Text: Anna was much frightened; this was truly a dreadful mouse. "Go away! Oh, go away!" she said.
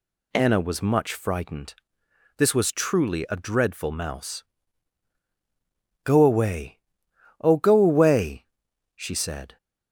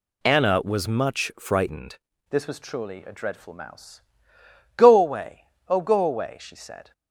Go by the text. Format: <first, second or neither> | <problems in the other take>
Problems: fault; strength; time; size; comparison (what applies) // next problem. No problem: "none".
first | changes voice at "this"; from 2.3 s on; 4.6 s long